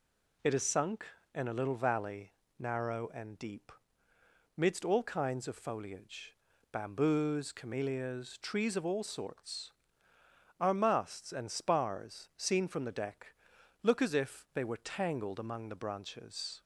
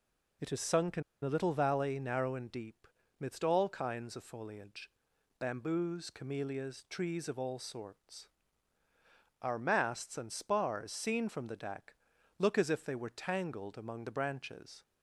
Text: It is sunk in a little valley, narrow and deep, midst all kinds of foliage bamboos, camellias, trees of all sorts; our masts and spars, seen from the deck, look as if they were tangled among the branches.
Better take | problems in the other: first | pauses between "in" and "a"; slight; at 1.0 s; 0.21 s long // pauses between "foliage" and "bamboos"; noticeable; at 4.9 s; 0.50 s long; also in the first

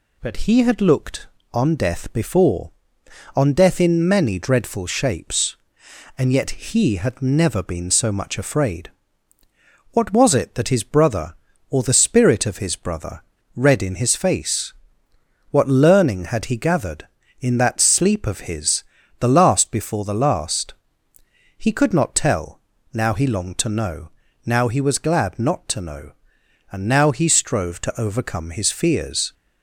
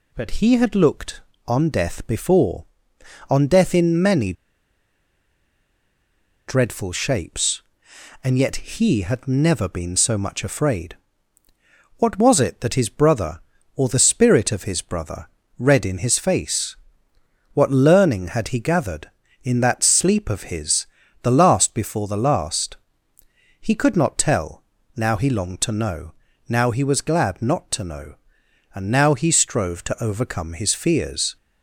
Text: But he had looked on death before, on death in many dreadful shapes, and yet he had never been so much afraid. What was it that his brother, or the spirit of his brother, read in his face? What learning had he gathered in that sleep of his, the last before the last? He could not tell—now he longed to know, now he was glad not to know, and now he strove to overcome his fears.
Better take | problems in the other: first | pauses between "many" and "dreadful"; strong; at 4.3 s; 2.1 s long

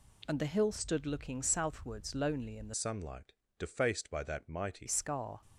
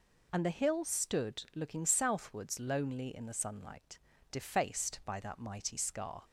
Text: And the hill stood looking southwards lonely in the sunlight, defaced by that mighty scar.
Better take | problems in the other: second | changes voice from "sunlight" to "mighty"; from 2.7 to 4.8 s; 2.1 s long

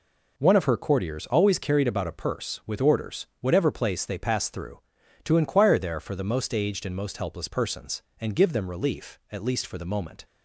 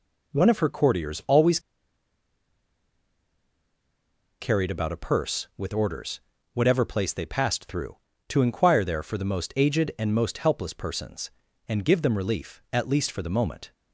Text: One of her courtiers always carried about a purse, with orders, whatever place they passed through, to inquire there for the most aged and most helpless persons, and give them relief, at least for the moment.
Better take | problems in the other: first | pauses between "always" and "carried"; strong; at 1.5 s; 2.8 s long

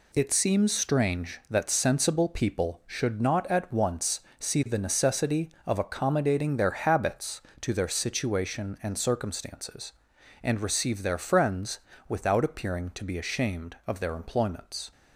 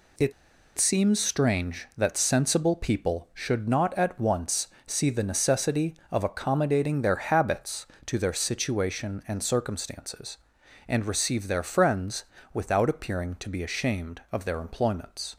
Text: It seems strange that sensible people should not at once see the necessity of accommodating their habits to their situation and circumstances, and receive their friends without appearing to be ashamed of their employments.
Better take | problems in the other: first | pauses between "It" and "seems"; at 0.3 s; 0.45 s long // pauses between "once" and "see"; slight; at 4.6 s; 0.20 s long; slight in the first // pauses between "friends" and "without"; slight; at 12.2 s; 0.28 s long; slight in the first

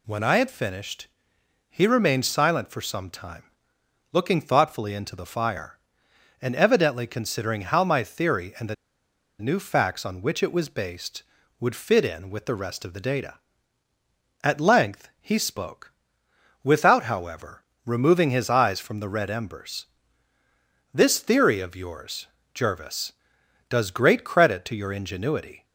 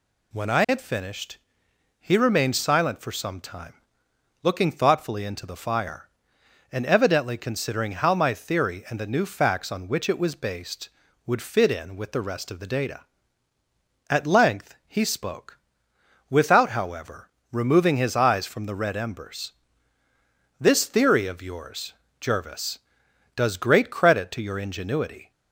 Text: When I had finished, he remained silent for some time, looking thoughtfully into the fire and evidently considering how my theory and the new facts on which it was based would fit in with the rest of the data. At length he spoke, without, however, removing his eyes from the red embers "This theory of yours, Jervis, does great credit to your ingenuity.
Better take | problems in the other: second | pauses between "the" and "new"; noticeable; at 8.7 s; 0.65 s long // pauses between "embers" and "This"; at 19.8 s; 1.0 s long; also in the second

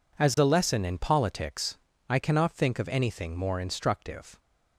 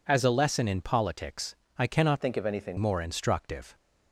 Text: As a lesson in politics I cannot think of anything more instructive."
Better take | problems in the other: first | pauses between "politics" and "I"; slight; at 1.5 s; 0.22 s long; slight in the first // changes voice from "think" to "anything"; from 2.2 to 2.7 s; 0.5 s long

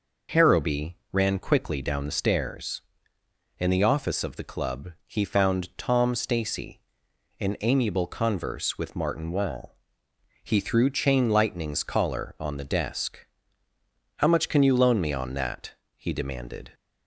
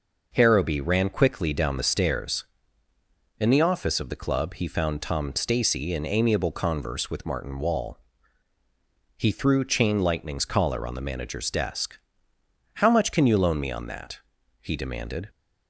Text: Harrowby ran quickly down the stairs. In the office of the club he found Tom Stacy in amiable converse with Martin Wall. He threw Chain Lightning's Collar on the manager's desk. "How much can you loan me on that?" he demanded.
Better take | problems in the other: second | pauses between "club" and "he"; slight; at 4.9 s; 0.16 s long // skips "manager's"; at 12.6 s

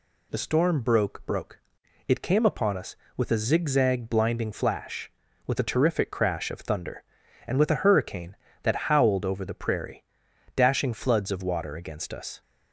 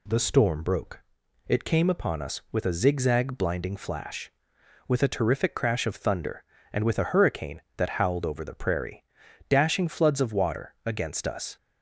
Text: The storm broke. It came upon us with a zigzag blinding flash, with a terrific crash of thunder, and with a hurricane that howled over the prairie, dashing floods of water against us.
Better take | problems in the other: second | says "broke" twice; at 1.2 s

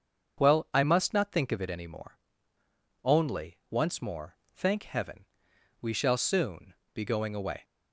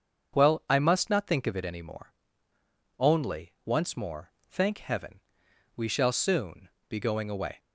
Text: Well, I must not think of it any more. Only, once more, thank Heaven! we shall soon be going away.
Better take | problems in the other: neither | starts louder than the rest; the same in both // pauses between "soon" and "be"; slight; the same in both

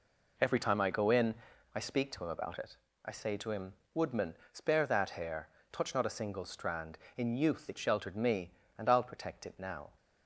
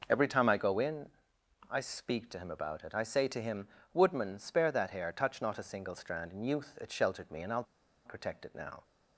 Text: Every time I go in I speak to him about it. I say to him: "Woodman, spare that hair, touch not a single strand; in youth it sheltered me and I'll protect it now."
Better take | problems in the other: first | pauses between "in" and "I"; noticeable; at 1.0 s; 0.64 s long; also in the first // pauses between "I'll" and "protect"; at 7.6 s; 0.42 s long

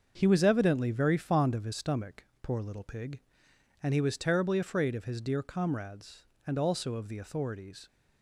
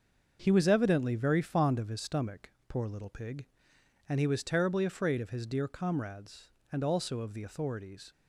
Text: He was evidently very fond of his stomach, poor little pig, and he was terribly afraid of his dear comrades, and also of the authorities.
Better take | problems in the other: neither | starts louder than the rest; the same in both

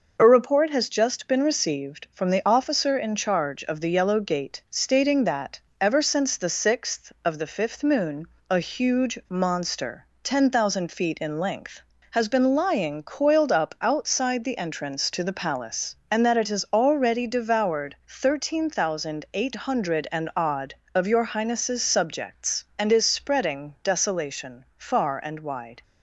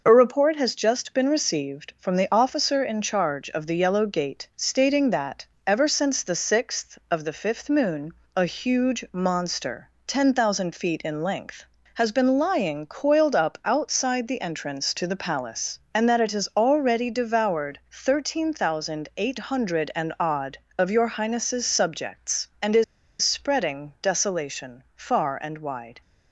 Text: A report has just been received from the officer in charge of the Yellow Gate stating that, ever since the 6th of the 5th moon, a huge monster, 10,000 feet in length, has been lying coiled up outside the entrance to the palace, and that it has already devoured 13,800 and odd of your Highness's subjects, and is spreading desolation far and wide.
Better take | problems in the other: first | pauses between "is" and "spreading"; at 22.8 s; 0.38 s long

